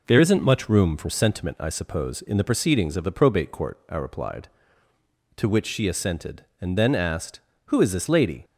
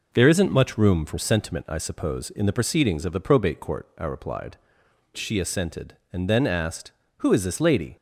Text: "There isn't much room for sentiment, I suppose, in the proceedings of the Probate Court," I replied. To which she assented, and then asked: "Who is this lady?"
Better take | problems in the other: first | skips "To which"; at 4.8 s

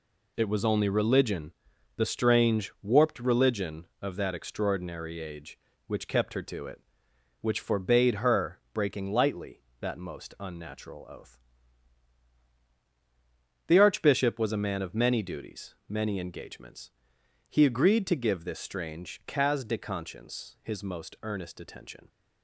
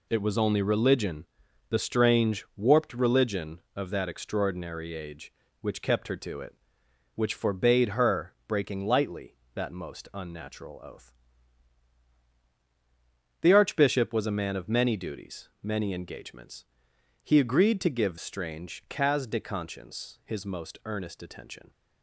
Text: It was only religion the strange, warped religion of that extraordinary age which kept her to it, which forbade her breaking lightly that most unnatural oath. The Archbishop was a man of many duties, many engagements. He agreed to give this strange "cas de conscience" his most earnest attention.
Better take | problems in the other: first | pauses between "religion" and "the"; at 1.2 s; 0.44 s long; also in the first // pauses between "her" and "breaking"; slight; at 8.3 s; 0.16 s long; slight in the first // skips "this"; at 18.1 s

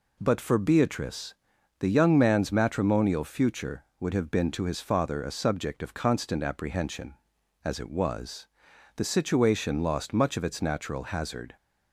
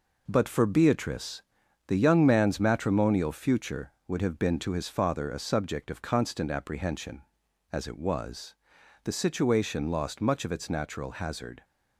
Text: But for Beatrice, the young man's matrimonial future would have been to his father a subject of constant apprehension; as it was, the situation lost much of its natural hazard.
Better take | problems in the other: first | gets quieter; throughout; 6.5 dB

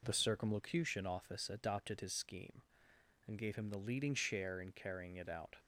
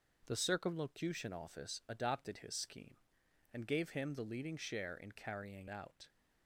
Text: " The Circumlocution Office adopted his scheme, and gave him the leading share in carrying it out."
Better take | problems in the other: first | starts louder than the rest; noticeable; until 1.2 s; 6 dB // skips "it"; at 5.6 s

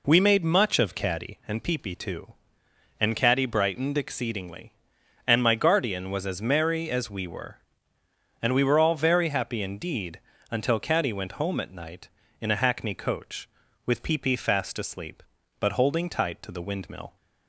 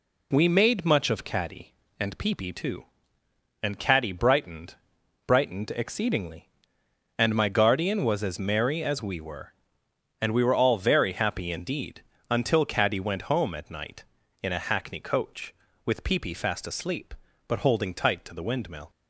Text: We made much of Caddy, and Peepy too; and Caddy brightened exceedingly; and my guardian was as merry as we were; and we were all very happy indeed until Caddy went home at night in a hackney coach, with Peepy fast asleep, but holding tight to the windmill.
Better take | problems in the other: first | says "brightened" twice; at 5.2 s // pauses between "indeed" and "until"; slight; at 12.0 s; 0.28 s long; slight in the first

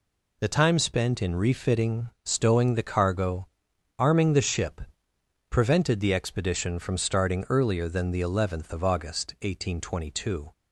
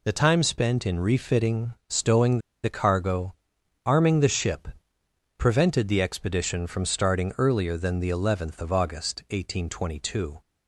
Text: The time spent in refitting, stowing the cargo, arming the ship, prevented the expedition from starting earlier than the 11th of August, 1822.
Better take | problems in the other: first | pauses between "stowing" and "the"; slight; at 2.3 s; 0.24 s long

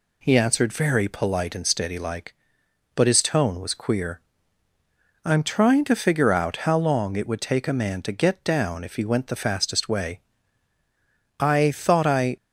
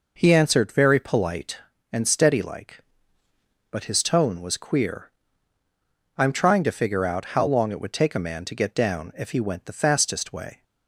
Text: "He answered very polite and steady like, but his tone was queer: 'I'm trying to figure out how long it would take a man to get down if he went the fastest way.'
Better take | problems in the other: second | goes on to say "I thought I"; noticeable; from 11.3 s on; 0.96 s long

